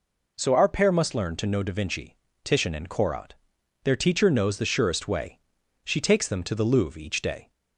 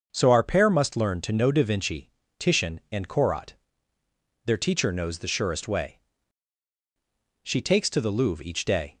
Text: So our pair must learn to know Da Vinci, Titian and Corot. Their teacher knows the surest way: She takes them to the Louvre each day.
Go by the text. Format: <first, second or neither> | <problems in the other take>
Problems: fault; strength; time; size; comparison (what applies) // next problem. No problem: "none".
first | starts louder than the rest; until 1.1 s; 6.5 dB // skips "them"; at 7.8 s